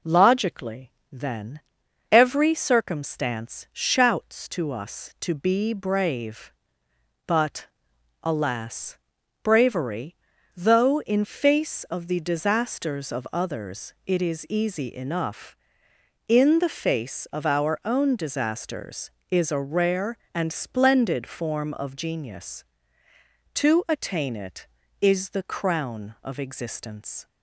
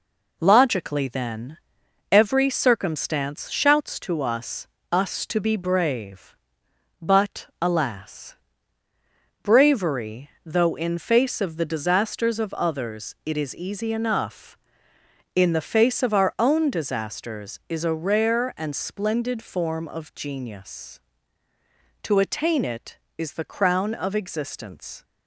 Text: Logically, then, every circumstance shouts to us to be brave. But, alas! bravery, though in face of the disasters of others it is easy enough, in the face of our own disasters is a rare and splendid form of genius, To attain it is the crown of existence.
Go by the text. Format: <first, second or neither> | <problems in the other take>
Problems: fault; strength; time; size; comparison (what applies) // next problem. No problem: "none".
first | says "us" twice; at 4.9 s